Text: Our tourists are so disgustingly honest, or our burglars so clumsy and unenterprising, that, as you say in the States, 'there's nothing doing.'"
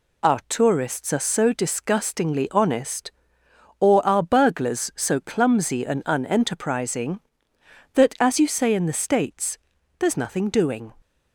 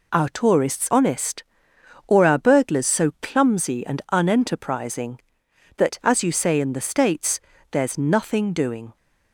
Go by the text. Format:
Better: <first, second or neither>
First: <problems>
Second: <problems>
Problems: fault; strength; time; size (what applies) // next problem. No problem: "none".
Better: first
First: none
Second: skips "are so disgustingly"; at 0.8 s